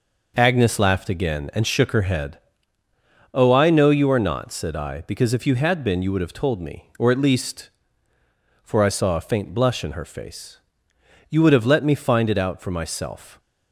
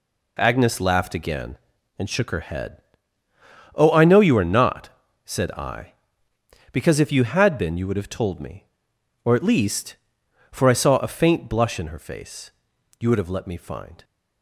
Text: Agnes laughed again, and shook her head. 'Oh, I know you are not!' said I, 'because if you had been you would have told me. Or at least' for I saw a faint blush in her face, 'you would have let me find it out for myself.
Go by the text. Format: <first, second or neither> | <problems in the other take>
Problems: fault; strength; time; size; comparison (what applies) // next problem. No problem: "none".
first | stops before "it out for myself"; at 14.0 s